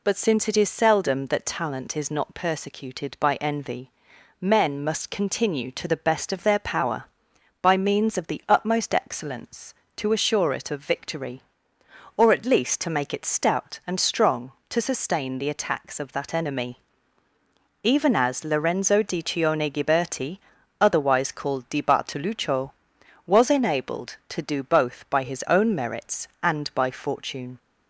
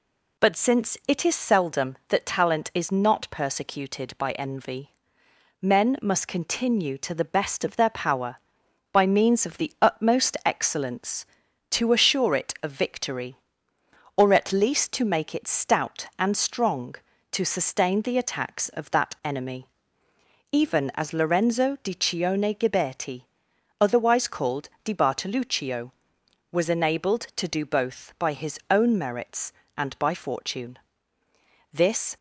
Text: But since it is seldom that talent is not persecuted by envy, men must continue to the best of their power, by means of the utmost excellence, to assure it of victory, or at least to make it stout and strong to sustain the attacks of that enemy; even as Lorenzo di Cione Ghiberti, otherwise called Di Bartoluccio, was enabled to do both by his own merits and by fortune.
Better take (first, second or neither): first